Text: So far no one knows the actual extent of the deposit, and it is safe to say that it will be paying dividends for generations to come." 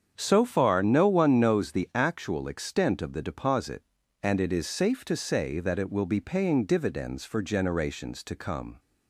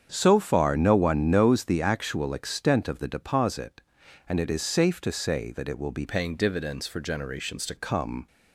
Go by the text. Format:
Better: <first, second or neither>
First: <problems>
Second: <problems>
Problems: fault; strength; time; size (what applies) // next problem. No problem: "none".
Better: first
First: starts louder than the rest; strong; until 1.1 s; 7.5 dB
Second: starts louder than the rest; strong; until 1.1 s; 7.5 dB // changes voice from "paying" to "to"; from 6.0 to 7.7 s; 1.7 s long